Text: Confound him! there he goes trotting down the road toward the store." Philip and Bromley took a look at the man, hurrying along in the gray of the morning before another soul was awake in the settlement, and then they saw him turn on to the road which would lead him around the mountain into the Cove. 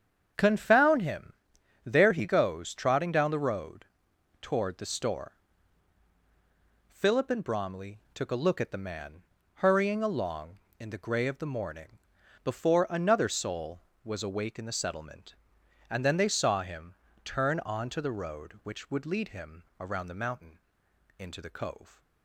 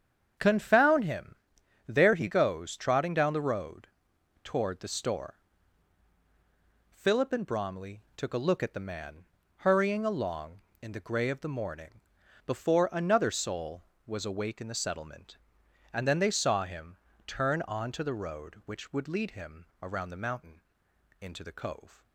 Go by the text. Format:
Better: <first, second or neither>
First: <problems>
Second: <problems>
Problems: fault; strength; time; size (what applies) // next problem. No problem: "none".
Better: neither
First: starts louder than the rest; strong; until 1.9 s; 8 dB // pauses between "road" and "toward"; noticeable; at 3.8 s; 0.56 s long // pauses between "morning" and "before"; noticeable; at 11.9 s; 0.46 s long // pauses between "him" and "turn"; slight; at 16.9 s; 0.28 s long // pauses between "him" and "around"; slight; at 19.6 s; 0.16 s long // pauses between "mountain" and "into"; noticeable; at 20.5 s; 0.58 s long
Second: starts louder than the rest; strong; until 1.9 s; 8 dB // pauses between "road" and "toward"; noticeable; at 3.8 s; 0.56 s long // pauses between "morning" and "before"; noticeable; at 12.0 s; 0.46 s long // pauses between "him" and "turn"; slight; at 16.9 s; 0.28 s long // pauses between "him" and "around"; slight; at 19.6 s; 0.16 s long // pauses between "mountain" and "into"; noticeable; at 20.6 s; 0.58 s long